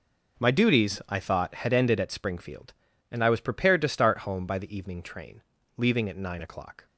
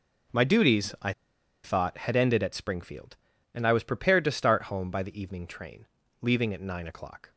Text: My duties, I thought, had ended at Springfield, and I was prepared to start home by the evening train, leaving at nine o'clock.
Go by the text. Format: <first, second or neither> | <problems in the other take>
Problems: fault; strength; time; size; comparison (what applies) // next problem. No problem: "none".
first | pauses between "I" and "thought"; noticeable; at 1.1 s; 0.52 s long